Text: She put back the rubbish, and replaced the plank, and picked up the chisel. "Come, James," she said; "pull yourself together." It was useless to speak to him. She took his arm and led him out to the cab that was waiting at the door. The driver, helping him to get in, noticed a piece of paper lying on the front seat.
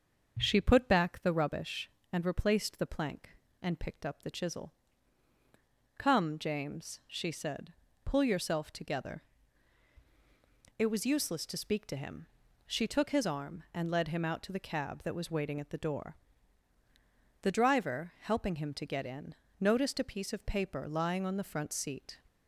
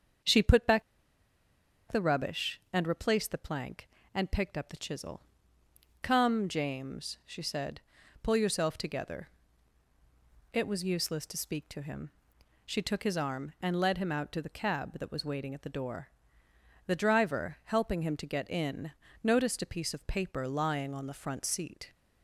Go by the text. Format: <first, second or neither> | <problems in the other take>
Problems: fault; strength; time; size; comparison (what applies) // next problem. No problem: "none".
first | starts louder than the rest; strong; until 2.3 s; 7 dB; also in the first // pauses between "back" and "the"; at 0.8 s; 1.0 s long